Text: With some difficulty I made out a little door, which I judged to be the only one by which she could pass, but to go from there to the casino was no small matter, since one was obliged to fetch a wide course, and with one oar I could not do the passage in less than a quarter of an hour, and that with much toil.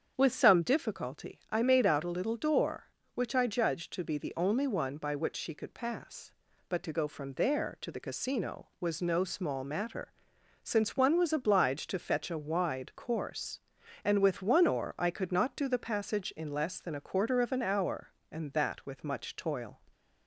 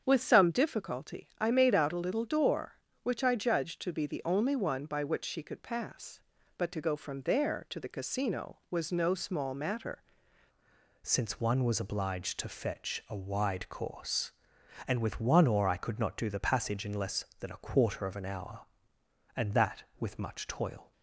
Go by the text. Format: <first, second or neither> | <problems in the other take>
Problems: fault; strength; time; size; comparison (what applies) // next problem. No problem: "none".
first | starts louder than the rest; strong; until 1.0 s; 7.5 dB; strong in the first // changes voice at "since"; from 11.0 s on; 9.9 s long